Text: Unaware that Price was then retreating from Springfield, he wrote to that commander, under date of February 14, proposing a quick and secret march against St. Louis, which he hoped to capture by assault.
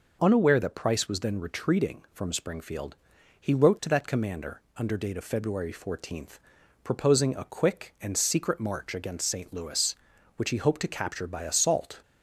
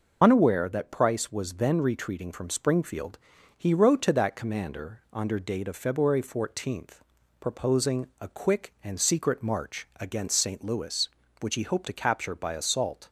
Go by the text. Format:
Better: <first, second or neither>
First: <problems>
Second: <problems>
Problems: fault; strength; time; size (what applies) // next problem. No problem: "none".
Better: first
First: none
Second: loses the start of "Unaware"; at 0.2 s; 45 ms